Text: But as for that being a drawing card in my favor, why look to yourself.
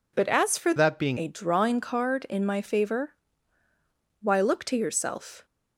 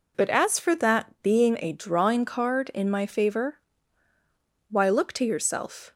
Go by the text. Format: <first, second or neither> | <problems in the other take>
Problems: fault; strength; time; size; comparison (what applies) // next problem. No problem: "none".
second | changes voice from "that" to "being"; from 0.7 to 1.1 s; 0.4 s long